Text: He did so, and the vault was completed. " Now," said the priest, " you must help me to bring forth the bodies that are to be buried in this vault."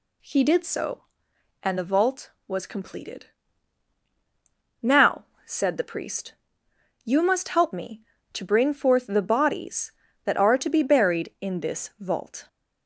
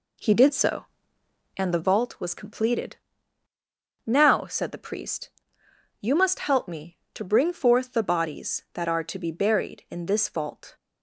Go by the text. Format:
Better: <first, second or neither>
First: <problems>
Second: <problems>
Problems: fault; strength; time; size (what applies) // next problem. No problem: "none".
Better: first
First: none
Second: starts louder than the rest; slight; until 2.1 s; 2.5 dB